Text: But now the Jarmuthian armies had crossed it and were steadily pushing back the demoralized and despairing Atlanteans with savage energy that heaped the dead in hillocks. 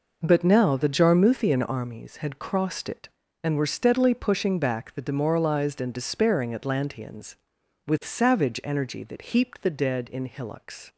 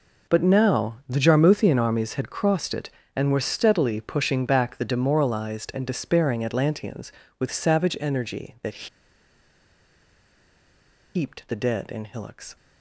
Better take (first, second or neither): first